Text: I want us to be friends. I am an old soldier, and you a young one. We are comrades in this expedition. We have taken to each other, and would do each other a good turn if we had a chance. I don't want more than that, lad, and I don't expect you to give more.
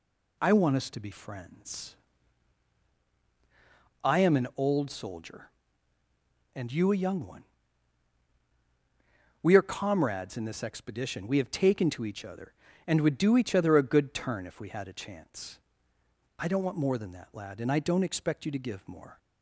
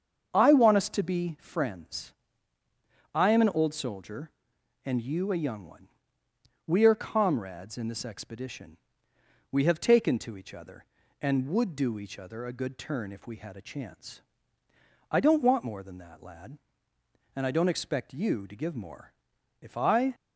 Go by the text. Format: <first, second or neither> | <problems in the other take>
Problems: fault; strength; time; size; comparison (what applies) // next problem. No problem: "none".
first | starts louder than the rest; until 1.3 s; 7 dB // goes on to say "If I"; from 19.6 s on; 0.54 s long